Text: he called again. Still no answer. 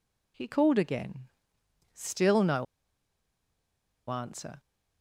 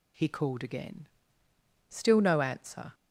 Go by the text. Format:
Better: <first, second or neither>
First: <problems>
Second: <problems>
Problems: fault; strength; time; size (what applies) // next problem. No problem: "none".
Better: second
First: pauses between "no" and "answer"; strong; at 2.6 s; 1.4 s long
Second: none